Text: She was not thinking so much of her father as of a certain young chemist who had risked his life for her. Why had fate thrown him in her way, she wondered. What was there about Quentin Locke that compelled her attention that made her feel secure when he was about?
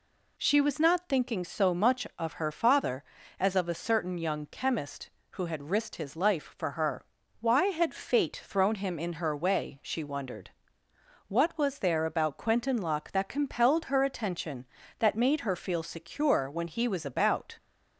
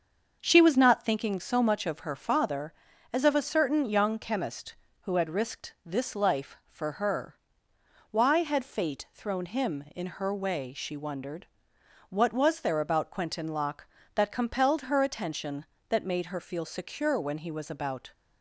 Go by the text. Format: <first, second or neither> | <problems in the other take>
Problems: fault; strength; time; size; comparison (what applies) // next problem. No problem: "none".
first | starts louder than the rest; until 1.4 s; 6.5 dB // says "this" for "his"; at 5.8 s